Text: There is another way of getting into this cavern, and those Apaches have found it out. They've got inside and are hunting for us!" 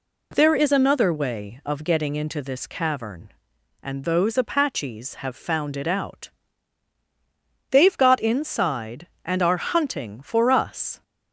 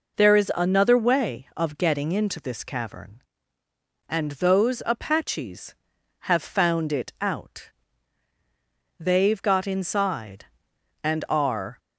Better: first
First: none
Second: stops before "hunting for us"; at 11.7 s

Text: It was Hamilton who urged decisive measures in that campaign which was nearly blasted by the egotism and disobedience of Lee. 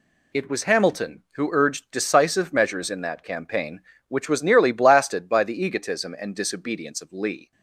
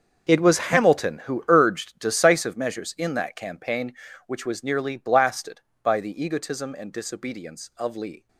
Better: first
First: none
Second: gets quieter; strong; throughout; 15.5 dB

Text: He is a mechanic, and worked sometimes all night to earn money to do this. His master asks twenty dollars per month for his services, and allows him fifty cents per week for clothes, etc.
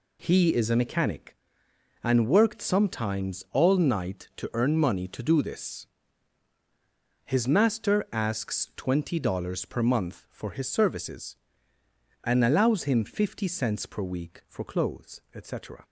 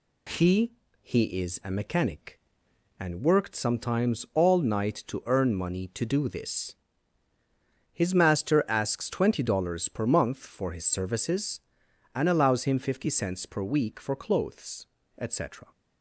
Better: first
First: none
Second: says "He" twice; at 1.0 s

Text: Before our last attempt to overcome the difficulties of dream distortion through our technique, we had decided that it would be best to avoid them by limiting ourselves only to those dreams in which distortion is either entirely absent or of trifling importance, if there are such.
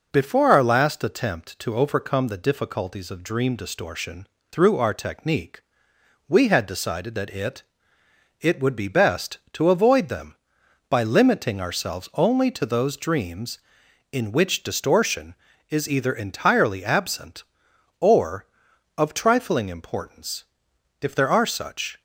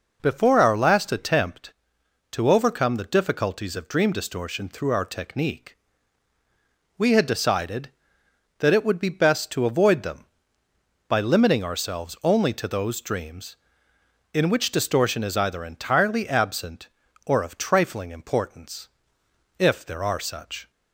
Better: second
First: pauses between "distortion" and "through"; slight; at 4.2 s; 0.24 s long // says "it" twice; at 8.4 s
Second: none

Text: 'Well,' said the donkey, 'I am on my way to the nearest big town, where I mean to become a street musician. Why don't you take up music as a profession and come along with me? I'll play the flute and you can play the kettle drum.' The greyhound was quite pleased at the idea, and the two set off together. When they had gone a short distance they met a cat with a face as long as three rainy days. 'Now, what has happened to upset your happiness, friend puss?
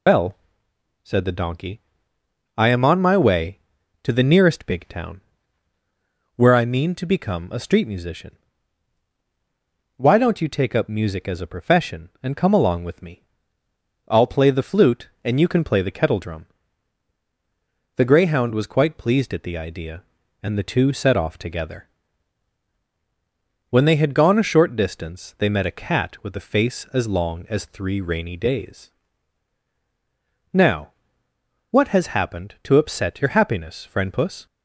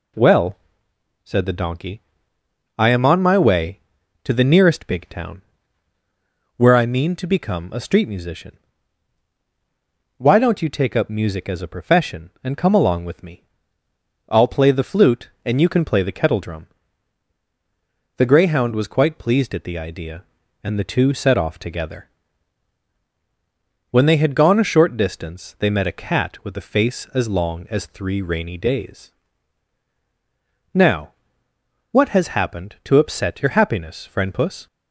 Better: second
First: loses the start of "Well"; at 0.0 s; 130 ms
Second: none

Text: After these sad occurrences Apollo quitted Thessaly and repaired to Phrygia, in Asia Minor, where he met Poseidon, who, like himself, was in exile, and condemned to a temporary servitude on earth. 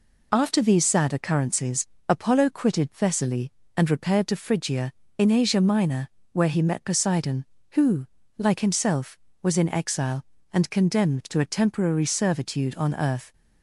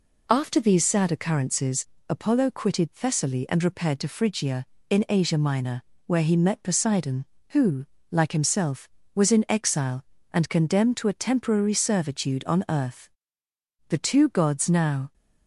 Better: first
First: pauses between "occurrences" and "Apollo"; slight; at 1.8 s; 0.22 s long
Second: pauses between "occurrences" and "Apollo"; slight; at 1.8 s; 0.24 s long // goes on to say "The two gods now"; noticeable; from 13.8 s on; 1.2 s long

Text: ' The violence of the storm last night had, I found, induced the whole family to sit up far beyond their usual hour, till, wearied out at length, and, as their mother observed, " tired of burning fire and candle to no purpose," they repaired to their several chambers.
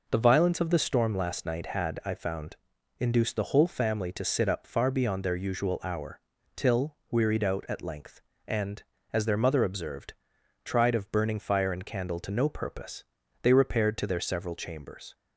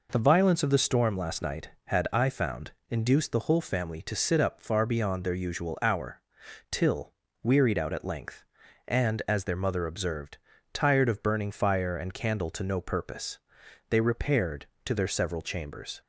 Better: second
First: says "tried" for "tired"; at 10.6 s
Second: none

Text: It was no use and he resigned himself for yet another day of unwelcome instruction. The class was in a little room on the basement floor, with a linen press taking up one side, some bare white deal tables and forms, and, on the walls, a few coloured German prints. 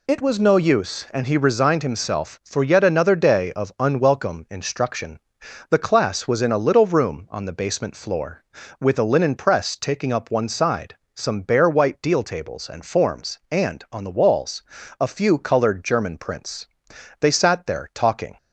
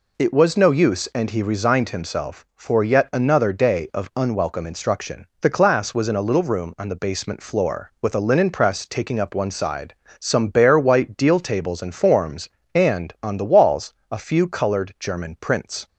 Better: second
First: goes on to say "They sat there talking"; noticeable; from 17.1 s on; 1.1 s long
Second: none

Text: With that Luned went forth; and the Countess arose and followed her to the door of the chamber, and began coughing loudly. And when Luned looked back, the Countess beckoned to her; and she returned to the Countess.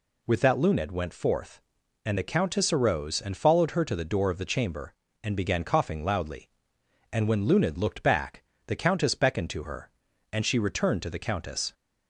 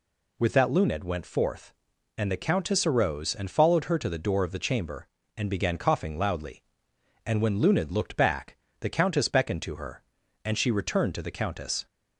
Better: neither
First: none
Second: none

